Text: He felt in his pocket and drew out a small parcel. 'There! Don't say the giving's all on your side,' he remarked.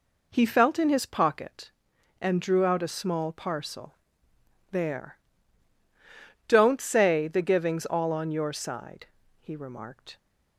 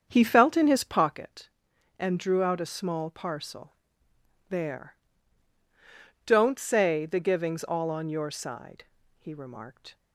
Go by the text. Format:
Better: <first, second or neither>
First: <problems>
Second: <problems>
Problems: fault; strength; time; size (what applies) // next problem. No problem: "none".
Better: first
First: none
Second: starts louder than the rest; strong; until 1.1 s; 7.5 dB